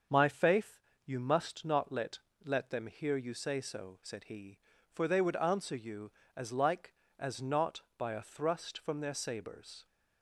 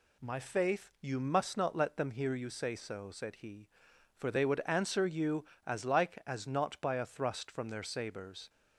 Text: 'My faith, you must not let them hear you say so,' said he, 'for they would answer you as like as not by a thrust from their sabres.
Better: second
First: starts louder than the rest; until 1.3 s; 7 dB // says "let" twice; at 2.4 s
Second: none

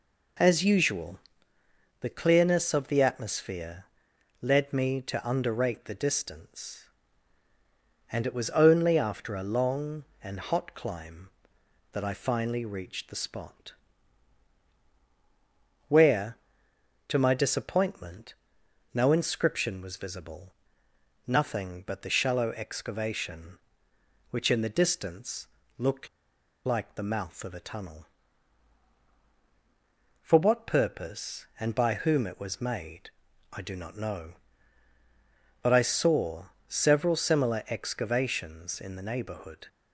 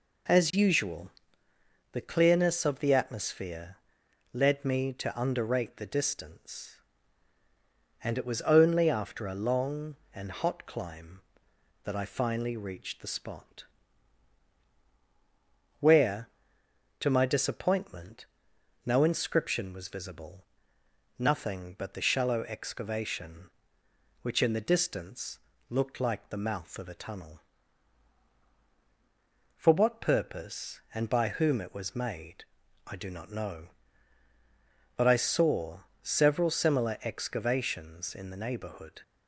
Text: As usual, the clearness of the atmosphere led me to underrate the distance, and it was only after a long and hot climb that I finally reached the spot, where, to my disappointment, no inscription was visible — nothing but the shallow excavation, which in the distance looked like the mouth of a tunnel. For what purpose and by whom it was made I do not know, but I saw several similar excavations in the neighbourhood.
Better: second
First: pauses between "atmosphere" and "led"; noticeable; at 3.8 s; 0.54 s long // pauses between "distance" and "looked"; slight; at 25.4 s; 0.32 s long // pauses between "looked" and "like"; noticeable; at 26.0 s; 0.57 s long // pauses between "made" and "I"; at 33.1 s; 0.42 s long // pauses between "saw" and "several"; slight; at 36.4 s; 0.22 s long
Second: pauses between "atmosphere" and "led"; noticeable; at 3.7 s; 0.54 s long // pauses between "distance" and "looked"; slight; at 25.3 s; 0.32 s long // pauses between "made" and "I"; at 32.4 s; 0.42 s long // pauses between "saw" and "several"; slight; at 35.7 s; 0.22 s long

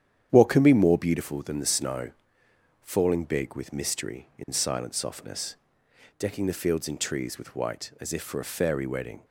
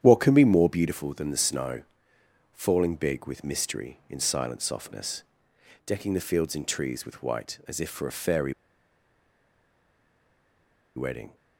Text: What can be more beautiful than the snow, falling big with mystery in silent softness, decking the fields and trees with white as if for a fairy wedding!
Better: first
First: starts louder than the rest; strong; until 1.3 s; 9.5 dB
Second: starts louder than the rest; strong; until 1.0 s; 9.5 dB // pauses between "fairy" and "wedding"; strong; at 8.5 s; 2.4 s long

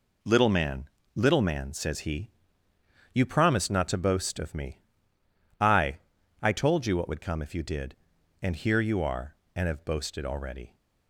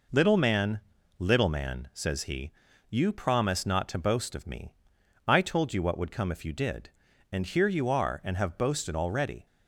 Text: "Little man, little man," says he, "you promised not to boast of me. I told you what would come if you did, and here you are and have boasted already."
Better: second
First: says "I" twice; at 6.4 s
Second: none

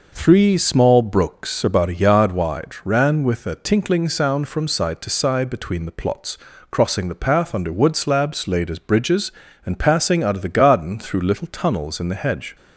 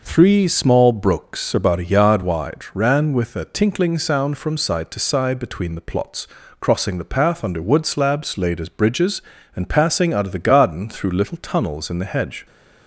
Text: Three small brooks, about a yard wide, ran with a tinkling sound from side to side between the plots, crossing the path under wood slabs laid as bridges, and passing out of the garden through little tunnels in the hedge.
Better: neither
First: none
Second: none

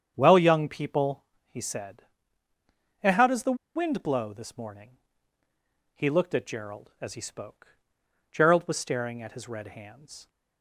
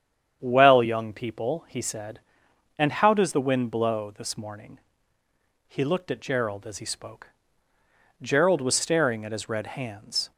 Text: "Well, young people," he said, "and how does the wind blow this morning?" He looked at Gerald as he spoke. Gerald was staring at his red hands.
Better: second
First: starts louder than the rest; strong; until 1.1 s; 8 dB // pauses between "the" and "wind"; slight; at 3.5 s; 0.19 s long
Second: starts louder than the rest; strong; until 1.4 s; 8.5 dB

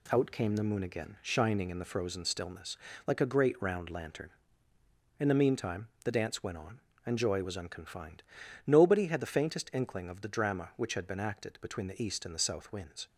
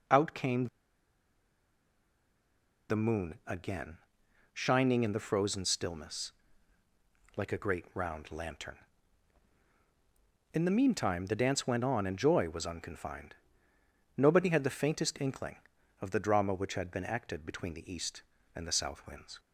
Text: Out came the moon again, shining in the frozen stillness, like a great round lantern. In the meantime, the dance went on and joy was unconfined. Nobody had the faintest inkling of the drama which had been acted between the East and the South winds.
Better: first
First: none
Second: pauses between "came" and "the"; strong; at 0.6 s; 2.2 s long

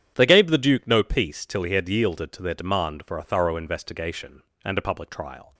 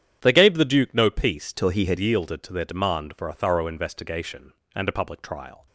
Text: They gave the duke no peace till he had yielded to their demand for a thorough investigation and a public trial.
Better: first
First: starts louder than the rest; strong; until 1.1 s; 9.5 dB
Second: starts louder than the rest; strong; until 1.2 s; 9.5 dB // changes voice from "till" to "had"; from 1.5 to 1.9 s; 0.4 s long

